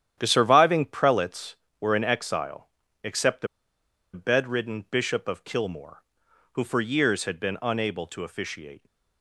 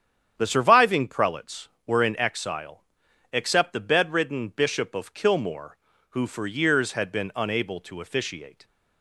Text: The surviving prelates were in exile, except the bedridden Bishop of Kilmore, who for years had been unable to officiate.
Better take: second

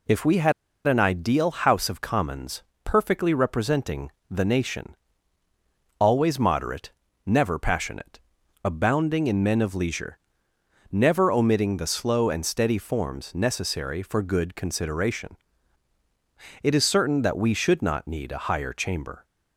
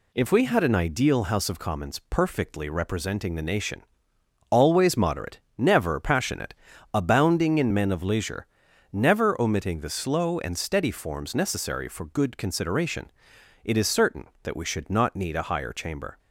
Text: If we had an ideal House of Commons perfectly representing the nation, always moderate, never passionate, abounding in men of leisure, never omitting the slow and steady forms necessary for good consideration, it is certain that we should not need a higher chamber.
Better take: second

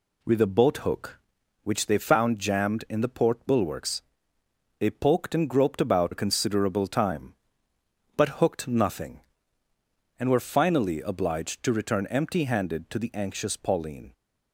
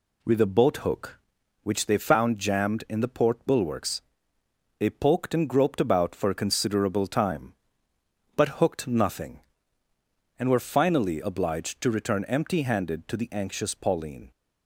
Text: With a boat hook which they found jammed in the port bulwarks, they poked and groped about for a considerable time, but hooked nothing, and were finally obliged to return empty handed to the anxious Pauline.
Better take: second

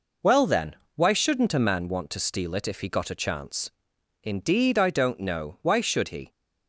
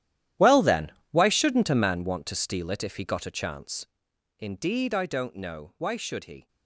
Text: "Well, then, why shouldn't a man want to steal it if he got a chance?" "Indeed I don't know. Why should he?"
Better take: first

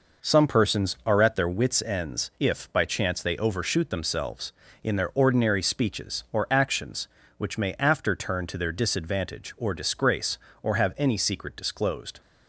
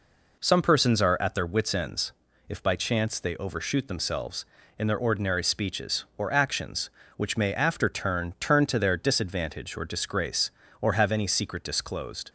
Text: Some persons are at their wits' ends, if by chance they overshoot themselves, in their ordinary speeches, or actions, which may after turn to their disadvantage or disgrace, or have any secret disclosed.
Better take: first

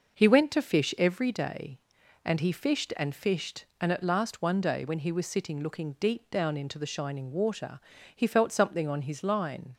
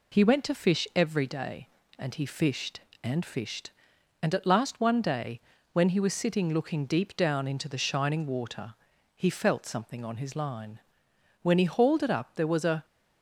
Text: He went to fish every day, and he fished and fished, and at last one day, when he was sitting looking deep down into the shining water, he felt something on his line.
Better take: first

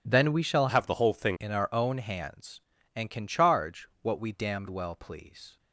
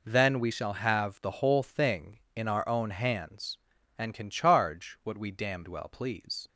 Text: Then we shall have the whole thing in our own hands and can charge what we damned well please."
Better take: second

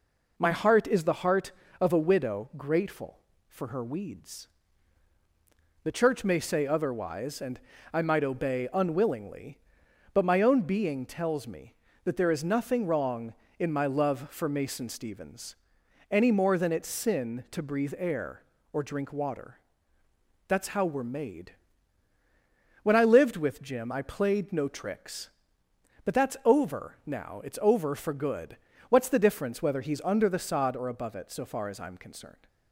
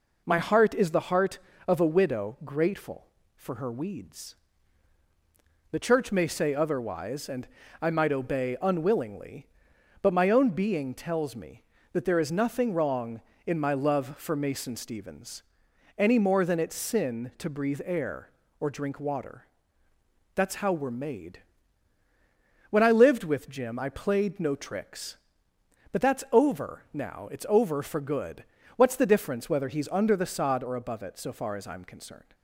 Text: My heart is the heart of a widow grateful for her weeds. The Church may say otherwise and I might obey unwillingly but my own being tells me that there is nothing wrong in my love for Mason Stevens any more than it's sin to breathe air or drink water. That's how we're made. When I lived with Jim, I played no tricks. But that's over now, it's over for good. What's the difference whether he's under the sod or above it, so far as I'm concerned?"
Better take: neither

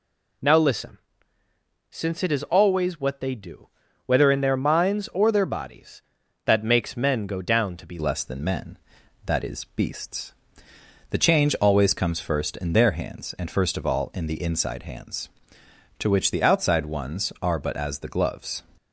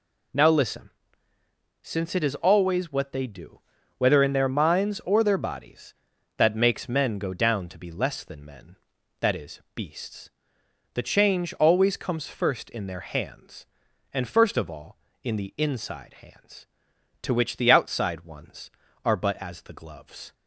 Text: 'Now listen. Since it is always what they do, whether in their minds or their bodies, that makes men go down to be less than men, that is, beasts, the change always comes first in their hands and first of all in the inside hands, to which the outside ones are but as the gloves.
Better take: second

